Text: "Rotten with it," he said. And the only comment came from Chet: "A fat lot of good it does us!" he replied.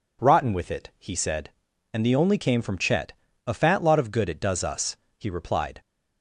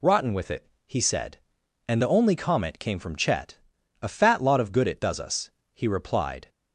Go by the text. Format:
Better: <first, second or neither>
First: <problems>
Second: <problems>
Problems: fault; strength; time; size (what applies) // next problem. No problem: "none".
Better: second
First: skips "comment"; at 2.3 s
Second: none